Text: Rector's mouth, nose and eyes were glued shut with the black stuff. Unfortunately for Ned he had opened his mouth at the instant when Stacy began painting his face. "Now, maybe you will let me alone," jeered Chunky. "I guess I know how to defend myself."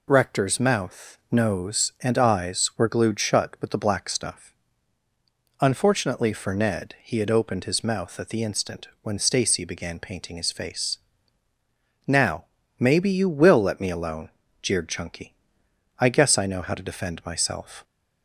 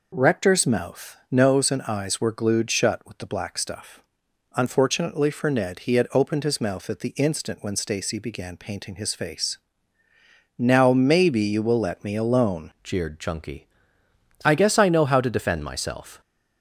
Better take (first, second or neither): first